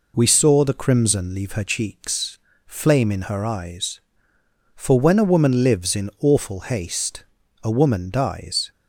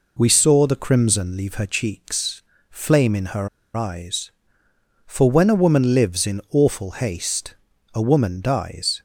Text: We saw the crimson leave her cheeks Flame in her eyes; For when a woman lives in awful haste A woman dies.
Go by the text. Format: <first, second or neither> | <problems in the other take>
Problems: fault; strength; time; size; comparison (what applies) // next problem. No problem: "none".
first | pauses between "cheeks" and "Flame"; slight; at 2.4 s; 0.30 s long; slight in the first // pauses between "her" and "eyes"; slight; at 3.4 s; 0.28 s long // pauses between "haste" and "A"; at 7.5 s; 0.40 s long; also in the first